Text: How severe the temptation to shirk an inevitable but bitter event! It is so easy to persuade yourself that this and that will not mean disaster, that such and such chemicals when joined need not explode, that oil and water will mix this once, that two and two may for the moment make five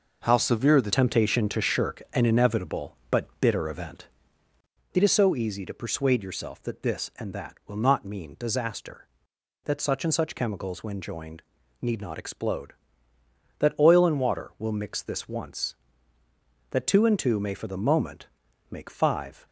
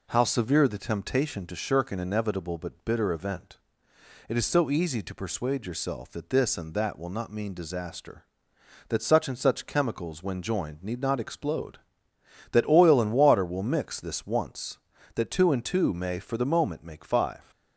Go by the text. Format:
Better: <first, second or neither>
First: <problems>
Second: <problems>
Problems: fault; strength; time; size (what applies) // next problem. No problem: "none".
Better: second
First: changes voice at "temptation"; from 0.9 s on; 18.5 s long // pauses between "joined" and "need"; at 11.4 s; 0.38 s long // pauses between "moment" and "make"; at 18.2 s; 0.42 s long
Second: none